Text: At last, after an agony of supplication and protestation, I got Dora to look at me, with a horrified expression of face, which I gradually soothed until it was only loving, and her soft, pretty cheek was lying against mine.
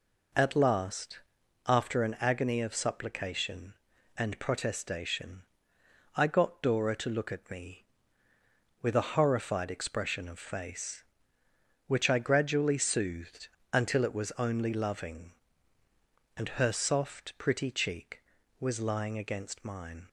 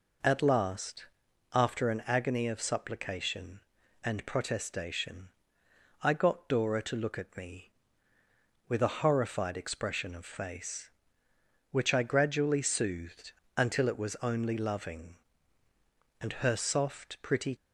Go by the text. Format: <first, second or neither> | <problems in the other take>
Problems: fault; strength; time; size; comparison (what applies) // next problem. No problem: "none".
first | pauses between "soothed" and "until"; slight; at 13.3 s; 0.24 s long; slight in the first // stops before "cheek was lying against mine"; at 17.5 s